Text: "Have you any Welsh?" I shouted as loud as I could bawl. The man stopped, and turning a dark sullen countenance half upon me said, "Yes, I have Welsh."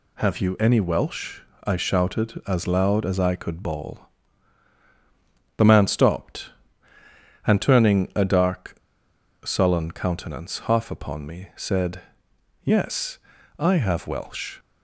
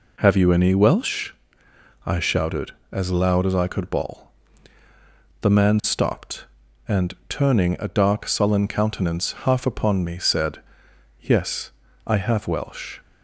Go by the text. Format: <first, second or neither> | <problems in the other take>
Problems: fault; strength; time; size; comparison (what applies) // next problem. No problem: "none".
second | pauses between "dark" and "sullen"; noticeable; at 8.7 s; 0.67 s long